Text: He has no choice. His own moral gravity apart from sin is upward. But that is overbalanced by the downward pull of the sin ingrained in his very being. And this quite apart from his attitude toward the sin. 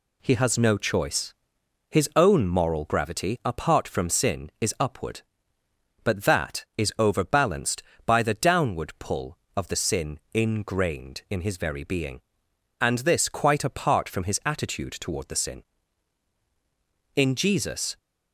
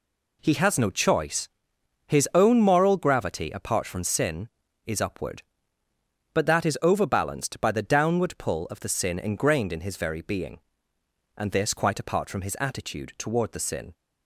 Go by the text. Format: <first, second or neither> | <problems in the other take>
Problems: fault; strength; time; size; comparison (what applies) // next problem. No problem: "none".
second | goes on to say "In Jesus"; noticeable; from 17.1 s on; 0.82 s long